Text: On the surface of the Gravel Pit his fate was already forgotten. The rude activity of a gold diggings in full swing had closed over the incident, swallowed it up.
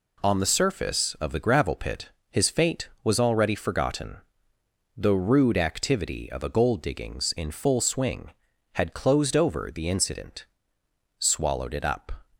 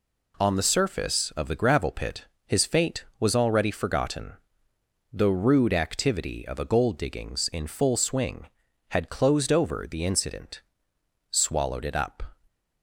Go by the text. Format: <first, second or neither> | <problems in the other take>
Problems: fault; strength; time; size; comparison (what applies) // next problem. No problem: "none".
neither | pauses between "Pit" and "his"; slight; the same in both